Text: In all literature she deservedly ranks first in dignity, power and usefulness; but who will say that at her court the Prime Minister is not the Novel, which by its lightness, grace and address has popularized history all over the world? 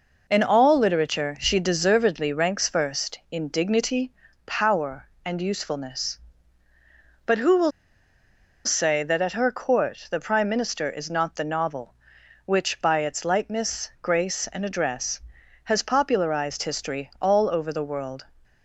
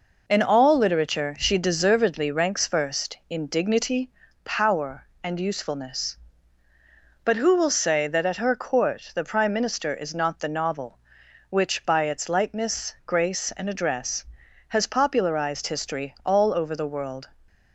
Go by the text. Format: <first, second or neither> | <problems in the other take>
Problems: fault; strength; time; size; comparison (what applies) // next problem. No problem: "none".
second | pauses between "will" and "say"; noticeable; at 7.7 s; 0.94 s long